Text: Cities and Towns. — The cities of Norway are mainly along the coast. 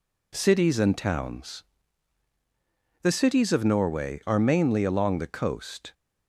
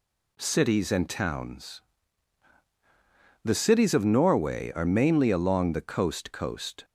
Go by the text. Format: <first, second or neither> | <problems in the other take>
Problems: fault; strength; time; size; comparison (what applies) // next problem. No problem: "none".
first | says "coast" twice; at 6.3 s